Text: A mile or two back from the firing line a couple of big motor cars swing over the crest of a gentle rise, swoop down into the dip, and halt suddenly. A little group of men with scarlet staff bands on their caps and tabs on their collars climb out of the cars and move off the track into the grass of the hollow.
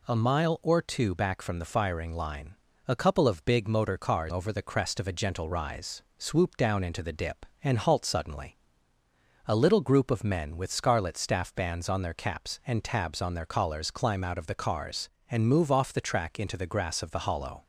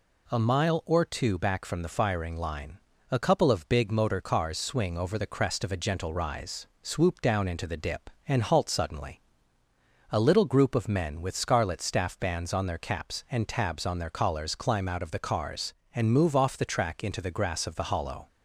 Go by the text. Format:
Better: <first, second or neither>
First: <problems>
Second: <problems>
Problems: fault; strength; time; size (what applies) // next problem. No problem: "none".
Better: second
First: pauses between "line" and "a"; slight; at 2.5 s; 0.32 s long // skips "swing"; at 4.3 s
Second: pauses between "line" and "a"; slight; at 2.7 s; 0.32 s long